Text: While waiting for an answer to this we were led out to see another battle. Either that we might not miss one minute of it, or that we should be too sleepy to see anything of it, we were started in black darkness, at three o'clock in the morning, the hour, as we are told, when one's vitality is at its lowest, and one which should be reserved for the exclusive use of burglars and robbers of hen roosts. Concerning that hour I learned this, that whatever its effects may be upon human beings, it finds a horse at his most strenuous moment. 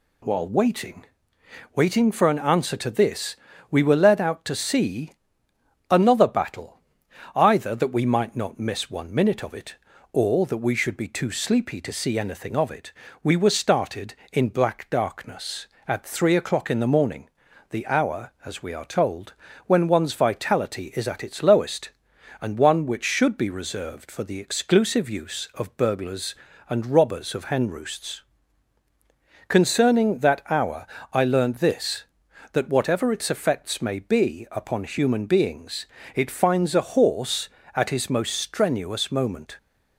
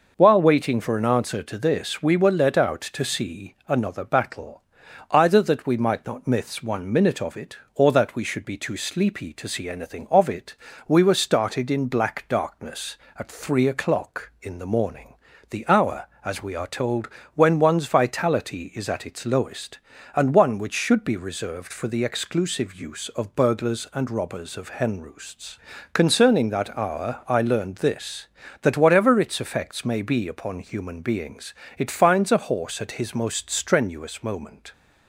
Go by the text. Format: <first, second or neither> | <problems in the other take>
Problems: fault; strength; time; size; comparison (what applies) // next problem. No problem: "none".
second | says "waiting" twice; at 1.7 s // pauses between "this" and "we"; slight; at 3.3 s; 0.34 s long // pauses between "see" and "another"; noticeable; at 5.1 s; 0.80 s long // pauses between "hour" and "I"; slight; at 30.8 s; 0.26 s long